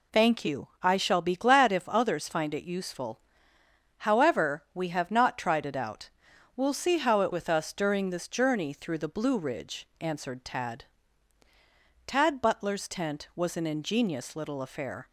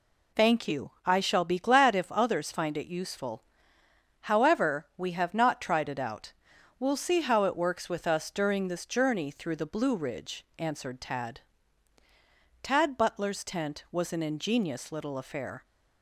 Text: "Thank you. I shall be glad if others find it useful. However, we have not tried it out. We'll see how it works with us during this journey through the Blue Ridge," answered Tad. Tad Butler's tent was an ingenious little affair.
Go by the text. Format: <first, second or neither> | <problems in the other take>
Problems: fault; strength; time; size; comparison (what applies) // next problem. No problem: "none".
second | skips "works"; at 7.3 s